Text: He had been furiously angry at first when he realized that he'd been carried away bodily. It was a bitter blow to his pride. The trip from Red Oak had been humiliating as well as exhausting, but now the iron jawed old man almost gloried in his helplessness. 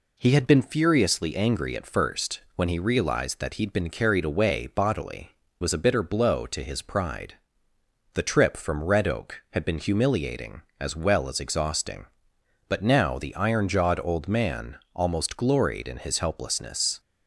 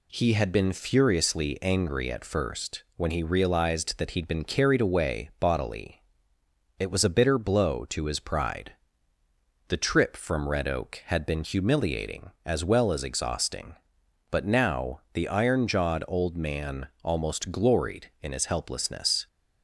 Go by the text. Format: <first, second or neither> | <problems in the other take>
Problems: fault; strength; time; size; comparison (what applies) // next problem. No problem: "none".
second | skips "It"; at 5.4 s // pauses between "man" and "almost"; slight; at 14.7 s; 0.18 s long; slight in the second